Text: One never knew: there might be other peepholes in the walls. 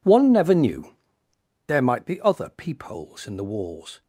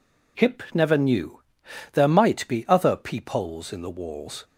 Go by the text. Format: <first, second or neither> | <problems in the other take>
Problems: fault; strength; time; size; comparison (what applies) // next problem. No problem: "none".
first | says "Hip" for "One"; at 0.3 s